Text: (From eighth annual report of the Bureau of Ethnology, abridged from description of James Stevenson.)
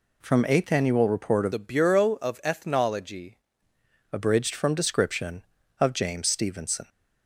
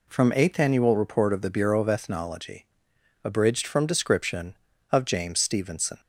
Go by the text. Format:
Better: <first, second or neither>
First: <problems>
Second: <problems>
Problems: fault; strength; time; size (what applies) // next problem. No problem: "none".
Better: second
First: changes voice from "the" to "Ethnology"; from 1.5 to 3.3 s; 1.8 s long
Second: none